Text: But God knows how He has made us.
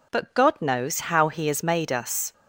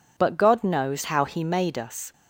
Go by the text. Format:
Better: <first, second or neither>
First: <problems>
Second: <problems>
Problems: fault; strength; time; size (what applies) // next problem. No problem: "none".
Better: first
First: none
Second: skips "has"; at 1.4 s